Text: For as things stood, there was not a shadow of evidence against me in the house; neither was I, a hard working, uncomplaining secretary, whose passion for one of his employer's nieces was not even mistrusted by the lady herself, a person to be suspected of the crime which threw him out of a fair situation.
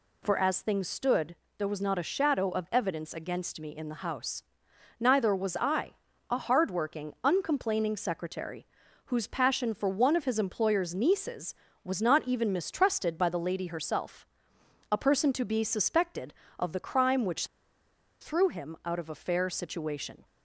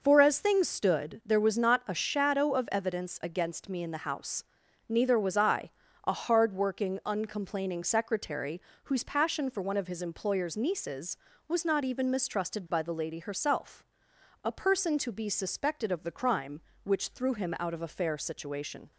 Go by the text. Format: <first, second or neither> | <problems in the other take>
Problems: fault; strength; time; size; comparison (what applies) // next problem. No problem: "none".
second | pauses between "which" and "threw"; noticeable; at 17.4 s; 0.73 s long